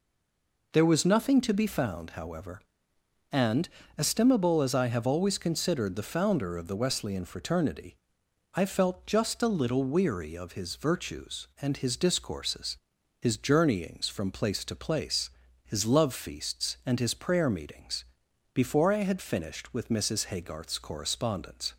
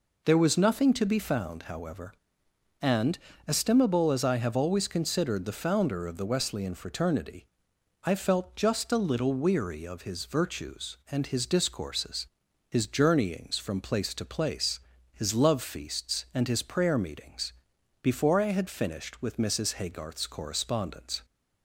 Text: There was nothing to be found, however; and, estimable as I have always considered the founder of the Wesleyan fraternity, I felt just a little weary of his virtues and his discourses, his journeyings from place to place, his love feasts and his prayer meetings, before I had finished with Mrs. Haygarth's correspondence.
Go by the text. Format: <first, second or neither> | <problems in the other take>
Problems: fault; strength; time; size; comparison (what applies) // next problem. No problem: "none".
second | stays silent before the first word; slight; until 0.7 s; 0.7 s long